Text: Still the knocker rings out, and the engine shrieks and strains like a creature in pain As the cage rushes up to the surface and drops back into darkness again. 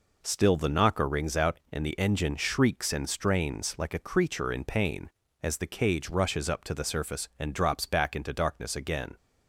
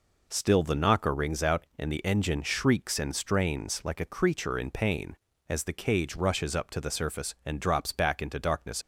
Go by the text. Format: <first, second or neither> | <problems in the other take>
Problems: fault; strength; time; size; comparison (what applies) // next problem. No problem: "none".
first | stops before "again"; at 8.8 s